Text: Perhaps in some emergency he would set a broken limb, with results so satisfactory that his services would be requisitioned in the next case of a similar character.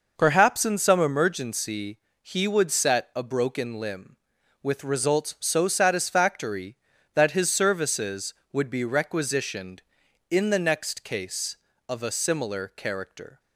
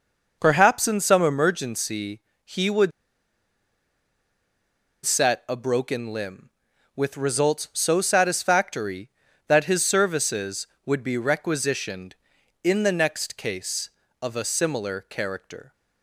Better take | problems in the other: first | pauses between "emergency" and "he"; slight; at 2.2 s; 0.24 s long; slight in the first // pauses between "would" and "set"; strong; at 2.9 s; 2.1 s long

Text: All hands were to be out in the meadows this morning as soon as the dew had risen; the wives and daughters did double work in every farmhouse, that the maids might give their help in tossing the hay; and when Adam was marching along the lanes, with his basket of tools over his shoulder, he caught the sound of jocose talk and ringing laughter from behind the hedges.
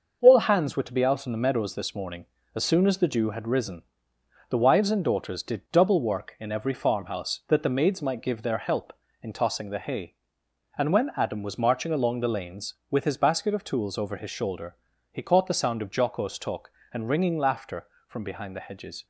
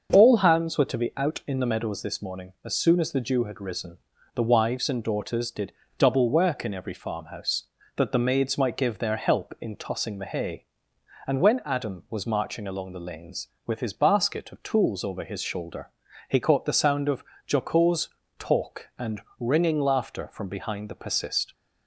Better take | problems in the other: first | starts louder than the rest; until 1.1 s; 6.5 dB // pauses between "did" and "double"; slight; at 5.7 s; 0.28 s long // pauses between "of" and "jocose"; slight; at 17.2 s; 0.26 s long // pauses between "jocose" and "talk"; slight; at 18.0 s; 0.28 s long // pauses between "and" and "ringing"; slight; at 19.2 s; 0.18 s long // says "persist" for "hedges"; at 20.9 s

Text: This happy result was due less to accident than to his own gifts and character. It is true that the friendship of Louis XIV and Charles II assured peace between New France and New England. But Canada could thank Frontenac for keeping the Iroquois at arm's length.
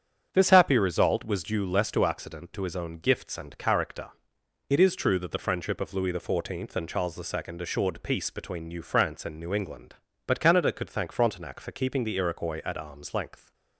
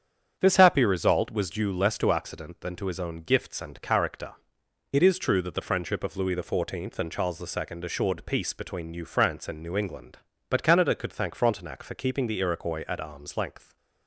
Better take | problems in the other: second | starts louder than the rest; strong; until 1.3 s; 8 dB; strong in the second // skips "than"; at 2.5 s

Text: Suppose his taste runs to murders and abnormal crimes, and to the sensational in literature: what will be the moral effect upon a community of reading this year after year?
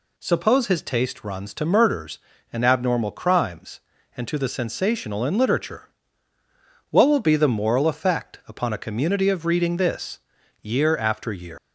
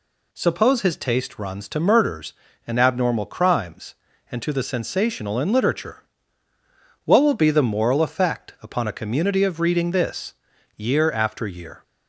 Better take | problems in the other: second | pauses between "this" and "year"; at 10.2 s; 0.42 s long; also in the second // leaves "year" unfinished; at 11.5 s; 105 ms

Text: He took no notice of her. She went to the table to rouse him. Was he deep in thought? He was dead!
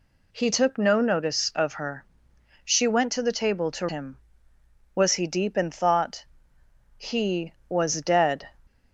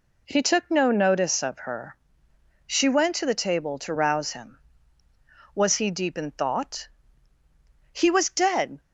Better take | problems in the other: second | skips "rouse"; at 3.8 s

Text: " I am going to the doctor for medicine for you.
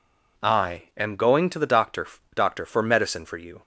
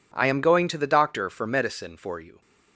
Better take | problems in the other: second | says "doctor" twice; at 2.3 s

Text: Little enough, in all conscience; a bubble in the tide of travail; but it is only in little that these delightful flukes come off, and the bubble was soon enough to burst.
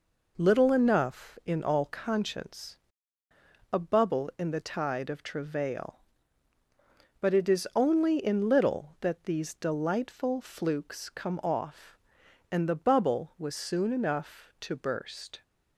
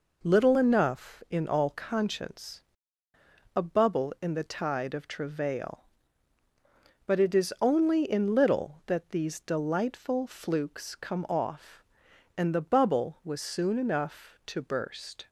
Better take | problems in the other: neither | none

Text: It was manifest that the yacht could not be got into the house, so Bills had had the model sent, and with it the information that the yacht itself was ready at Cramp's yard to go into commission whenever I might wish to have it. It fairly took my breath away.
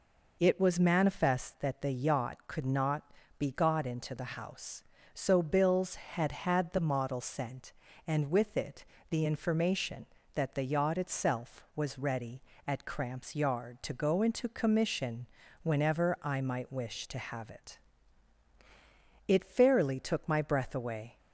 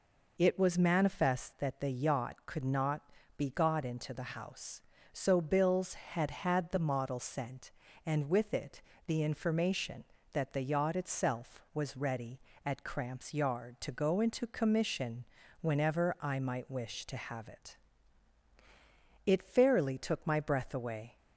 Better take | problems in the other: neither | pauses between "not" and "be"; slight; the same in both // pauses between "it" and "the"; slight; the same in both // pauses between "commission" and "whenever"; slight; the same in both

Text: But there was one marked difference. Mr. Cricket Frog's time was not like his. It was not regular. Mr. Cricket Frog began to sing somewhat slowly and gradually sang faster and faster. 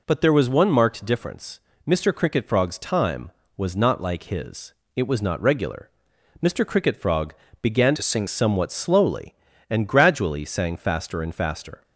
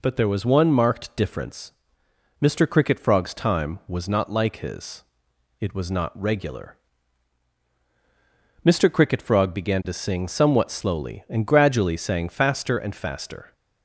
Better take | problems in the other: second | pauses between "Frog" and "began"; slight; at 7.3 s; 0.28 s long // changes voice from "to" to "sing"; from 7.9 to 8.2 s; 0.3 s long

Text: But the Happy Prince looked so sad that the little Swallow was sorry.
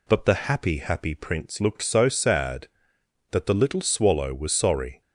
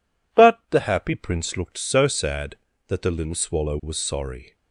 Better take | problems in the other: second | says "Happy" twice; at 0.7 s

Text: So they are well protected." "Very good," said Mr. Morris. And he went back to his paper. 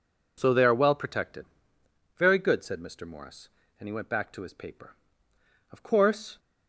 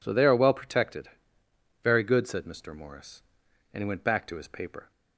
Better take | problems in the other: second | goes on to say "Of course"; noticeable; from 5.7 s on; 0.66 s long

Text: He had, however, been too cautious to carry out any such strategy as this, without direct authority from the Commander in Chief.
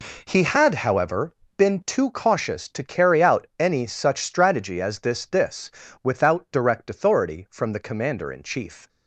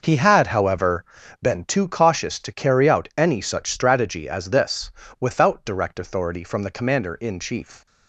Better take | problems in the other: second | says "this" twice; at 5.2 s

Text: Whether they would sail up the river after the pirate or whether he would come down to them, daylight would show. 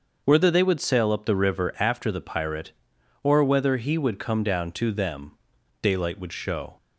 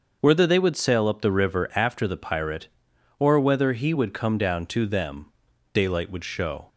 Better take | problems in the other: neither | starts louder than the rest; noticeable; the same in both

